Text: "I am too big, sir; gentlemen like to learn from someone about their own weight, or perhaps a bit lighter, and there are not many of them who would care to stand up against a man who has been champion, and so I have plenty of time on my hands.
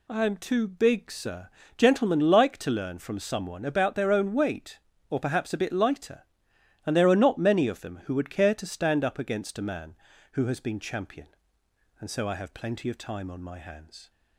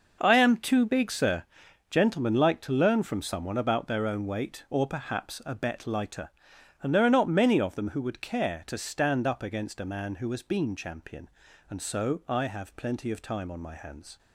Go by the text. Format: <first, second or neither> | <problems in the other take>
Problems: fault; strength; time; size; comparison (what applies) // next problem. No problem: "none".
first | says "bet" for "bit"; at 5.5 s